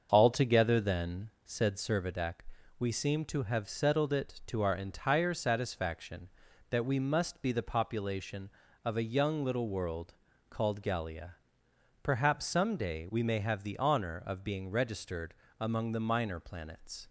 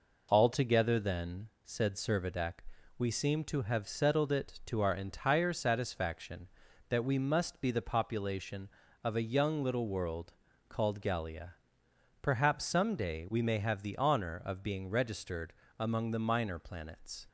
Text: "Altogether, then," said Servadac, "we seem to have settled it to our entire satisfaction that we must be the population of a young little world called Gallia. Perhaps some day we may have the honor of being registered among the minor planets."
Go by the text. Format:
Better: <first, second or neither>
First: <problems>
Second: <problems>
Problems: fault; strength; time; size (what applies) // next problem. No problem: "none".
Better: second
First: starts louder than the rest; until 1.9 s; 6.5 dB // pauses between "world" and "called"; slight; at 10.1 s; 0.34 s long // pauses between "registered" and "among"; slight; at 15.3 s; 0.28 s long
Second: pauses between "world" and "called"; slight; at 10.3 s; 0.34 s long // pauses between "registered" and "among"; slight; at 15.5 s; 0.28 s long